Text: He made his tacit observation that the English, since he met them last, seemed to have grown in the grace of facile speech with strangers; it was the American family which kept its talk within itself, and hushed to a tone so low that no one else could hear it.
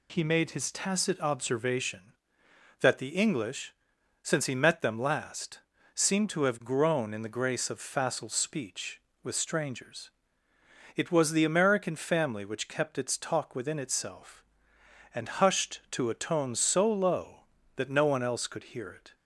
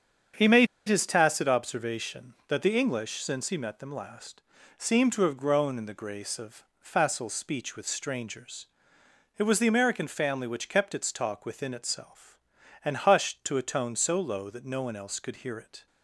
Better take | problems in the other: first | starts louder than the rest; strong; until 1.5 s; 7.5 dB // pauses between "made" and "his"; slight; at 0.6 s; 0.21 s long

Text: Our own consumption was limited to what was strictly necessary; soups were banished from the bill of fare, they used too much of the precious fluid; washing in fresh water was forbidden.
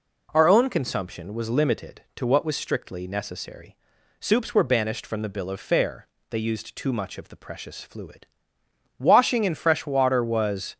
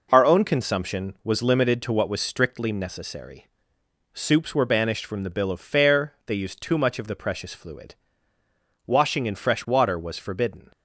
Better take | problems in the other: second | stops before "forbidden"; at 10.7 s

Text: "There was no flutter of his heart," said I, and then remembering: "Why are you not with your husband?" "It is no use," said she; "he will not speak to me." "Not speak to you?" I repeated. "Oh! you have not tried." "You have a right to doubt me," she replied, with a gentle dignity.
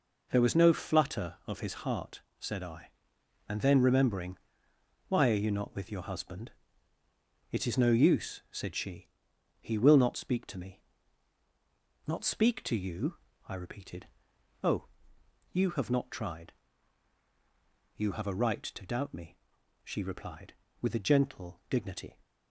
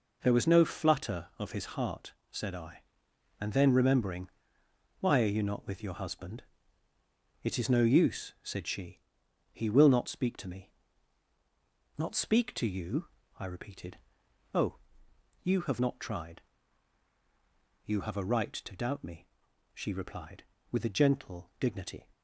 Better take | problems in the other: neither | none

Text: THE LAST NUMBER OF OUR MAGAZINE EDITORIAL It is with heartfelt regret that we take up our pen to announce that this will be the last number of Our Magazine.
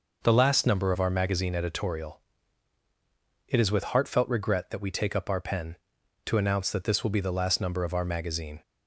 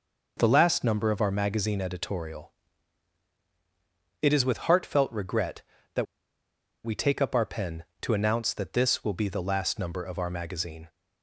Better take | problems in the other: first | pauses between "EDITORIAL" and "It"; strong; at 2.5 s; 1.7 s long; strong in the first // pauses between "that" and "we"; noticeable; at 6.0 s; 0.79 s long

